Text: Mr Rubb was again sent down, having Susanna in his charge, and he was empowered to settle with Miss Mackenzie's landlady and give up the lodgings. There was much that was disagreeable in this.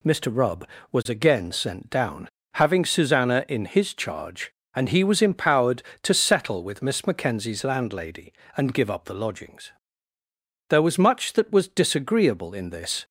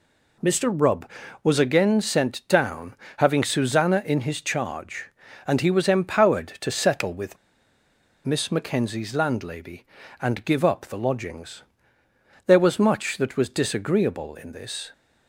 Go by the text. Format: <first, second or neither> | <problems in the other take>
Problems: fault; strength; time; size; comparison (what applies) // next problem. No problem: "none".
first | pauses between "with" and "Miss"; noticeable; at 7.3 s; 0.88 s long